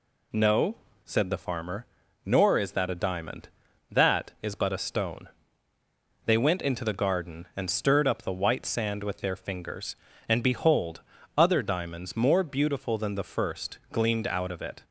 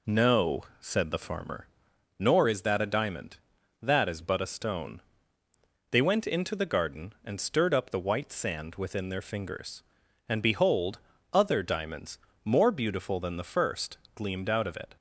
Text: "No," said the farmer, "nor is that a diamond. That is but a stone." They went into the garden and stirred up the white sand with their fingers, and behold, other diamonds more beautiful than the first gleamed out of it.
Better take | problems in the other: first | says "within" for "with"; at 8.7 s // pauses between "diamonds" and "more"; slight; at 12.1 s; 0.26 s long // pauses between "first" and "gleamed"; slight; at 13.9 s; 0.18 s long

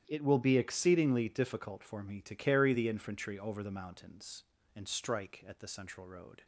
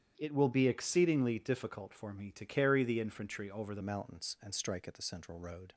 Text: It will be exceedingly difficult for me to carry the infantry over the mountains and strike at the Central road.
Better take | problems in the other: first | starts louder than the rest; strong; until 1.1 s; 10 dB; strong in the first // changes voice at "mountains"; from 3.8 s on; 1.9 s long

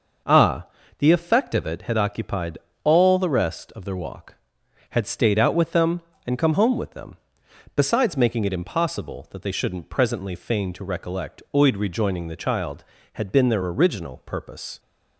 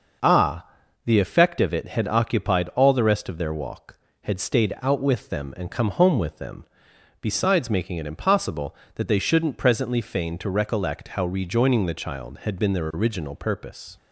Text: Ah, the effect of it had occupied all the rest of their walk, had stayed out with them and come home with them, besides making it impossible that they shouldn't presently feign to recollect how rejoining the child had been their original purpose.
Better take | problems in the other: second | pauses between "occupied" and "all"; slight; at 2.5 s; 0.24 s long // says "oid" for "how"; at 11.5 s

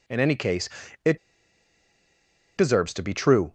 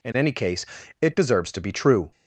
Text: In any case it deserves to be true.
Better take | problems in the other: second | pauses between "case" and "it"; slight; at 0.6 s; 0.36 s long; slight in the second // pauses between "it" and "deserves"; strong; at 1.1 s; 1.3 s long

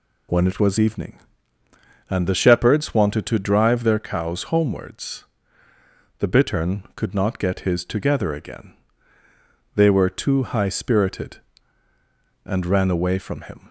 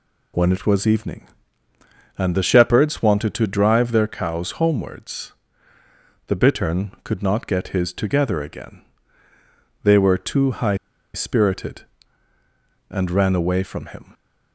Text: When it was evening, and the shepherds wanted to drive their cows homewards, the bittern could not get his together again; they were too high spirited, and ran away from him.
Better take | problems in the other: first | pauses between "high" and "spirited"; at 10.7 s; 0.39 s long

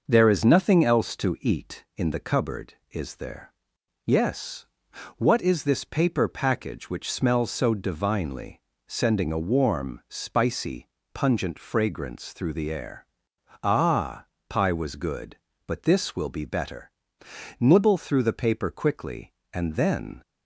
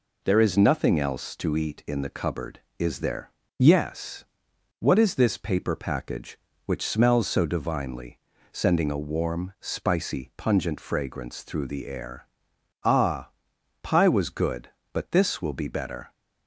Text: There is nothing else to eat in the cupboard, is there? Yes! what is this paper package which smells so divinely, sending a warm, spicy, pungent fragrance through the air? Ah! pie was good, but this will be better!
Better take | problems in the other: second | goes on to say "Nibble through the paper quickly and then"; strong; from 17.5 s on; 2.6 s long

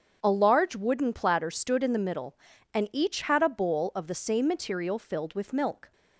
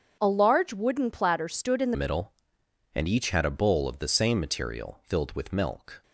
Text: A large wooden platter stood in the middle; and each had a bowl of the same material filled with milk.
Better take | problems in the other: first | starts louder than the rest; strong; until 1.2 s; 7 dB; strong in the first // changes voice at "middle"; from 1.9 s on; 4.1 s long

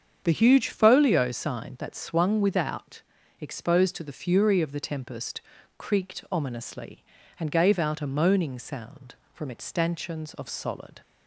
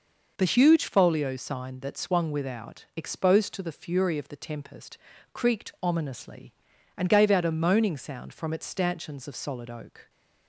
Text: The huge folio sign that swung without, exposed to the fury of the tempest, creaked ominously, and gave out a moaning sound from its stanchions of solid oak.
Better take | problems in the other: second | starts louder than the rest; strong; until 1.2 s; 7.5 dB // stops before "oak"; at 11.0 s

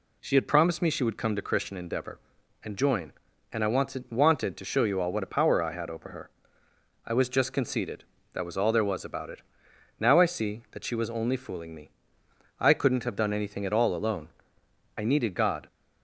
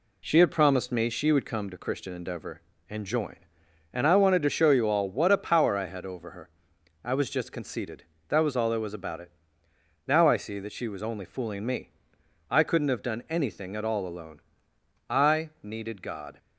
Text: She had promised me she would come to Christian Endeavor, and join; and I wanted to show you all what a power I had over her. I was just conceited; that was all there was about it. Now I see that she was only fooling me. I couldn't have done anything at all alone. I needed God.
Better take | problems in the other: second | says "wanted" twice; at 4.1 s

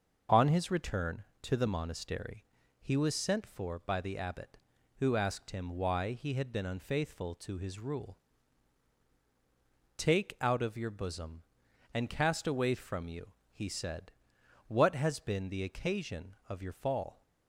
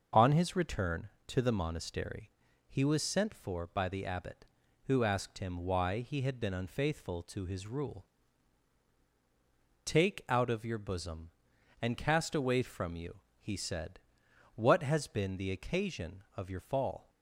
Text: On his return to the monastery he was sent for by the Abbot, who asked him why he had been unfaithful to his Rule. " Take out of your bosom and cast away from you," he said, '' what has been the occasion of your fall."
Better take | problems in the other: neither | starts louder than the rest; strong; the same in both // pauses between "monastery" and "he"; the same in both

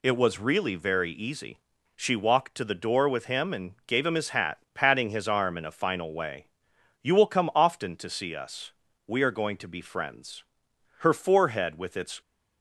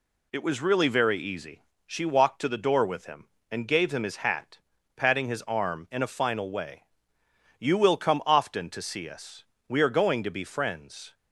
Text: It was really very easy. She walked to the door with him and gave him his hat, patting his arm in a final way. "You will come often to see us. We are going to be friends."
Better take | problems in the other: second | goes on to say "Her forehead with its"; noticeable; from 10.9 s on; 1.2 s long

